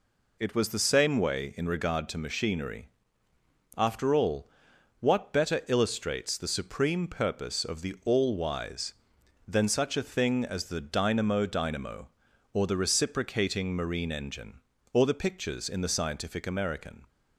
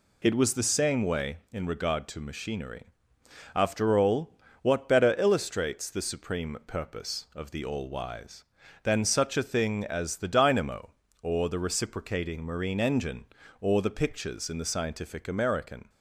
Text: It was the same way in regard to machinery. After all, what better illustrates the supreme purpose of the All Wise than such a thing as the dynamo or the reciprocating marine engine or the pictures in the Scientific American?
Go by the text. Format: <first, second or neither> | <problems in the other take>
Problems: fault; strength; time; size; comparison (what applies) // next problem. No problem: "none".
second | says "dynamo" twice; at 11.4 s